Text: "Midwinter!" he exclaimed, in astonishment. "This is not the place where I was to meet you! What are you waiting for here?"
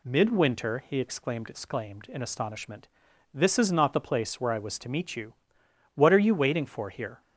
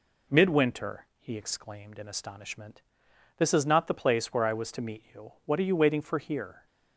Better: second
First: says "exclaimed" twice; at 1.4 s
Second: none

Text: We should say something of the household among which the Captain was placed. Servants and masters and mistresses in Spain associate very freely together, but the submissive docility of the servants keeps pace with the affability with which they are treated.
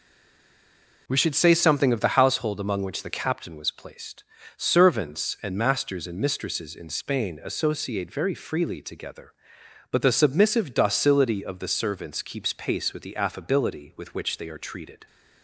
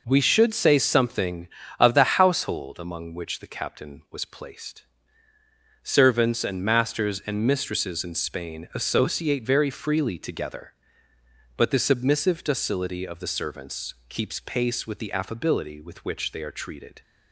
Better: second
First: stays silent before the first word; until 1.0 s; 1.0 s long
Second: none

